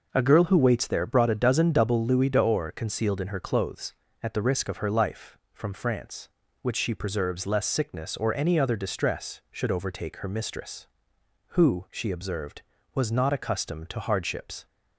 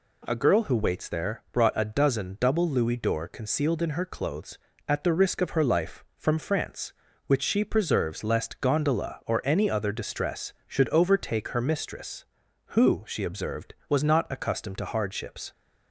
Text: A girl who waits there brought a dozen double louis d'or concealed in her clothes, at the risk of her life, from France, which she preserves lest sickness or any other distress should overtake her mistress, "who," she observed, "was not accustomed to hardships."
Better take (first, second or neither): first